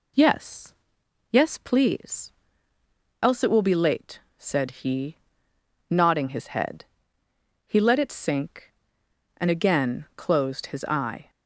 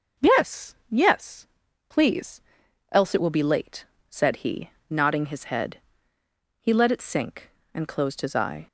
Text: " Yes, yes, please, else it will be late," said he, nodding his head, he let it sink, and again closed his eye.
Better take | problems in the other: first | starts louder than the rest; noticeable; until 1.3 s; 6 dB // skips "again"; at 7.8 s

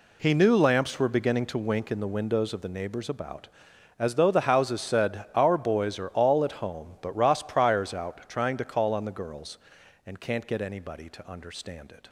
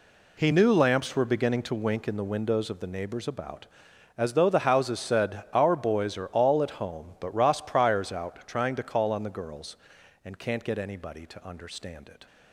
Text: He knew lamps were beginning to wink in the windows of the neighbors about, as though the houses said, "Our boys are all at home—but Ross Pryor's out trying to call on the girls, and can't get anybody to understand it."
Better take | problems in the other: neither | none

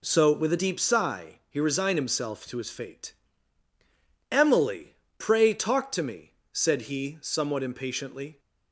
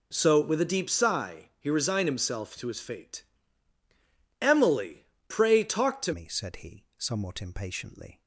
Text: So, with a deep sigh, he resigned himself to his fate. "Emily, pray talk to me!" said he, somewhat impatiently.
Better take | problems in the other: first | changes voice at "me"; from 6.1 s on; 2.1 s long

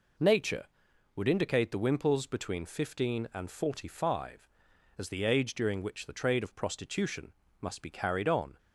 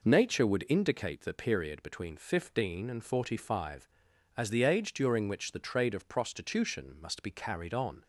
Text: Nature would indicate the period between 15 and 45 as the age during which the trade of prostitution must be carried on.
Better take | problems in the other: second | says "wimples" for "period"; at 1.7 s // pauses between "prostitution" and "must"; slight; at 7.3 s; 0.28 s long

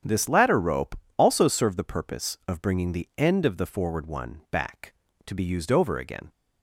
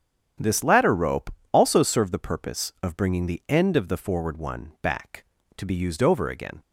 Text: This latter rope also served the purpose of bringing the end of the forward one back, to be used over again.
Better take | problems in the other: neither | starts louder than the rest; strong; the same in both // pauses between "rope" and "also"; slight; the same in both

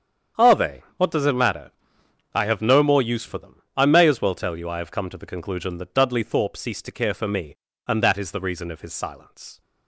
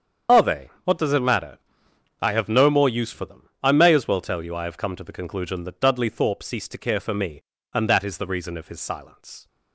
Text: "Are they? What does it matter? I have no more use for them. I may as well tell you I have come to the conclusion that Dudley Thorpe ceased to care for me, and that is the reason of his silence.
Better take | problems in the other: first | loses the start of "Are"; at 0.2 s; 55 ms // starts louder than the rest; strong; until 1.4 s; 8 dB; strong in the first

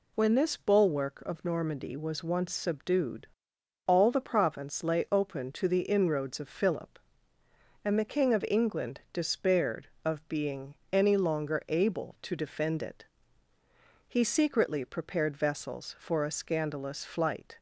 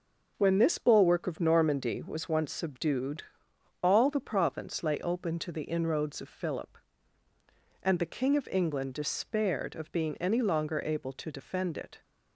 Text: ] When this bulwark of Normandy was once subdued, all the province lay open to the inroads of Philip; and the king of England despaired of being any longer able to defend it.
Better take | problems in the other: second | pauses between "being" and "any"; slight; at 10.7 s; 0.16 s long // goes on to say "He secretly prepared vessels for a scandalous flight"; strong; from 14.0 s on; 3.5 s long

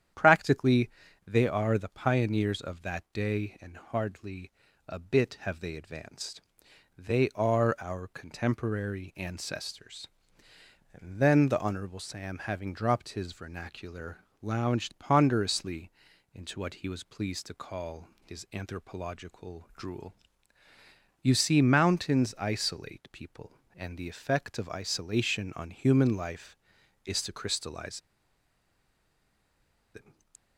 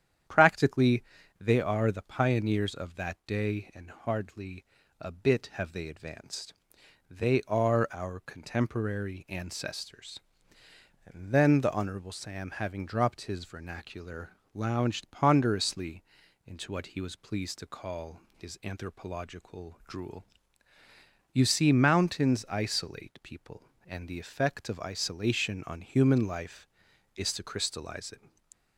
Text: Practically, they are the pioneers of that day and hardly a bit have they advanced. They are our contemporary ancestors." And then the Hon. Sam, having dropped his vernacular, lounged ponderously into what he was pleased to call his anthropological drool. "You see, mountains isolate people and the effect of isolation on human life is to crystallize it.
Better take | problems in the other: second | starts louder than the rest; strong; until 1.5 s; 9.5 dB; strong in the second // pauses between "hardly" and "a"; slight; at 4.5 s; 0.36 s long; slight in the second // pauses between "ponderously" and "into"; at 15.8 s; 0.44 s long; also in the second // pauses between "crystallize" and "it"; strong; at 28.0 s; 1.9 s long

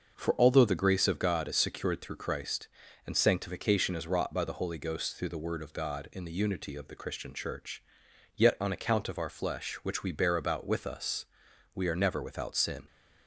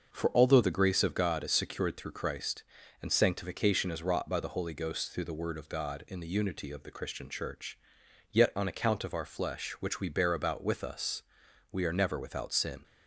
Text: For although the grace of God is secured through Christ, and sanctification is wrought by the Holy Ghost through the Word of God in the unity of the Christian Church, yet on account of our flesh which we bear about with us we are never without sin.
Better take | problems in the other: neither | starts louder than the rest; the same in both // pauses between "us" and "we"; noticeable; the same in both

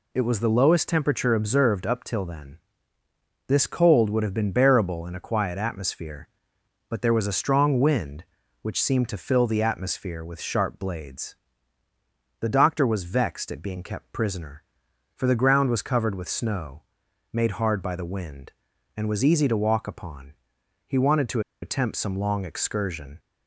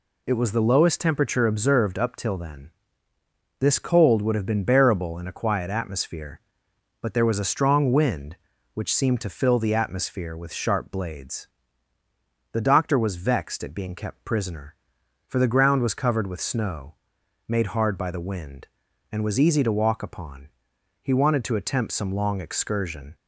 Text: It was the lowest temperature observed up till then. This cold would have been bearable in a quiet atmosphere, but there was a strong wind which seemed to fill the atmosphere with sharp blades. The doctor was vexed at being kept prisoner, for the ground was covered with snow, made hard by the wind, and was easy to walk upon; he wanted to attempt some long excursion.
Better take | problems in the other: second | pauses between "to" and "attempt"; slight; at 21.3 s; 0.22 s long

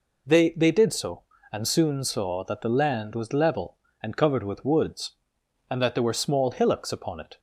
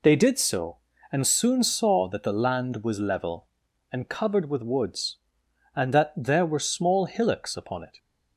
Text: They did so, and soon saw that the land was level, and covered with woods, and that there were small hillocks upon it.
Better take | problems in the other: second | says "They" twice; at 0.5 s

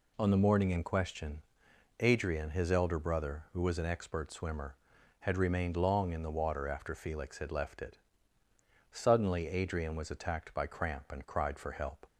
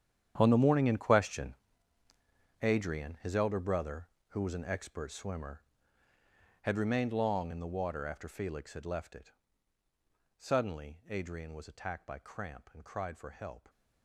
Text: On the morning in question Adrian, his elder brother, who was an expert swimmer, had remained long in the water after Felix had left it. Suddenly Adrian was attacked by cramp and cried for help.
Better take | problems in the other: first | gets quieter; strong; throughout; 15.5 dB // pauses between "question" and "Adrian"; at 1.5 s; 1.0 s long; noticeable in the first

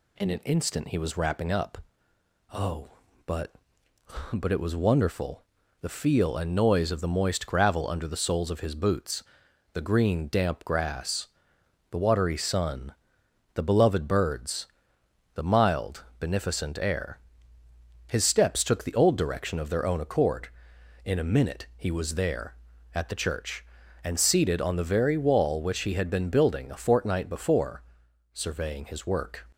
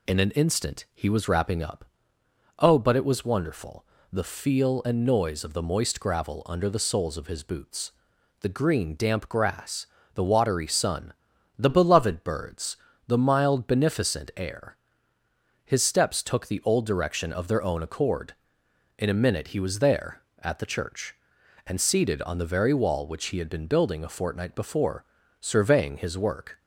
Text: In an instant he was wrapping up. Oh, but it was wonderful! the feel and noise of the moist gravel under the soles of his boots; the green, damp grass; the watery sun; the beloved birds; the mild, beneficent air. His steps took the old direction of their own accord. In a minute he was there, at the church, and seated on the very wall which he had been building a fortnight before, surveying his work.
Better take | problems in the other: second | says "but" twice; at 4.3 s

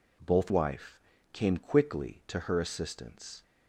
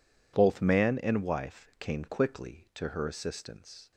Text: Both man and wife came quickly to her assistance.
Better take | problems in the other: second | skips "man and"; at 0.5 s // pauses between "wife" and "came"; slight; at 0.9 s; 0.36 s long

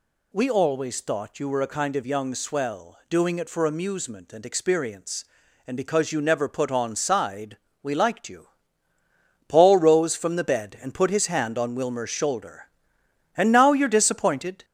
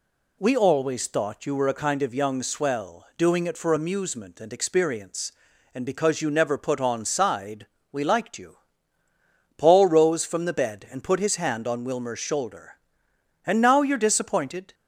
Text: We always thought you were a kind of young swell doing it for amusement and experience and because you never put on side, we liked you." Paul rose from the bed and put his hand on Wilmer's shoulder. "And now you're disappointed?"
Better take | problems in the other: second | gets louder; throughout; 3.5 dB

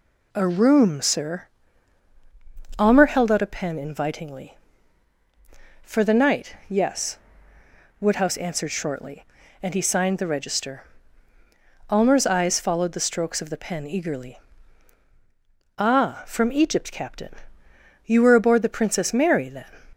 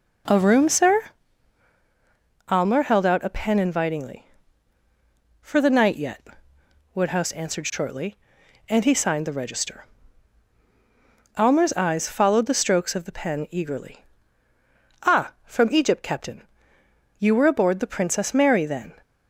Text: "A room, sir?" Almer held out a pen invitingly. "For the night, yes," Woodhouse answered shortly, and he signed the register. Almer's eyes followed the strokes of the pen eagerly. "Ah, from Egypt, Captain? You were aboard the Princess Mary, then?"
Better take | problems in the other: first | says "yet" for "yes"; at 5.9 s

